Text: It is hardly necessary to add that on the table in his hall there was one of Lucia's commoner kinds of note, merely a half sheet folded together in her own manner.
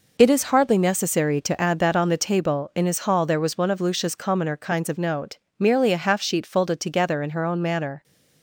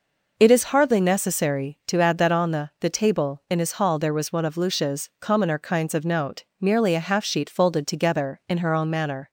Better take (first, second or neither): first